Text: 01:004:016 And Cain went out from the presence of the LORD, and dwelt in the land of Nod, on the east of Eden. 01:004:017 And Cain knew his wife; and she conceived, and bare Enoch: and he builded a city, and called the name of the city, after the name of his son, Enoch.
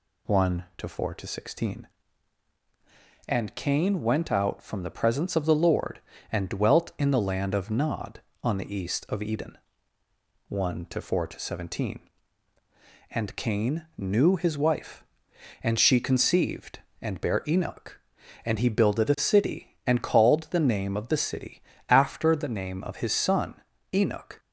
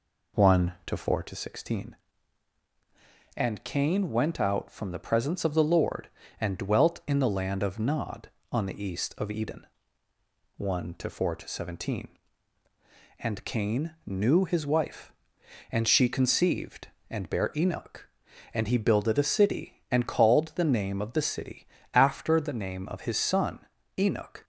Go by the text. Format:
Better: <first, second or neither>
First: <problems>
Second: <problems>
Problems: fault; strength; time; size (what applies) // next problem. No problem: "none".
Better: first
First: none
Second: starts louder than the rest; slight; until 1.3 s; 3.5 dB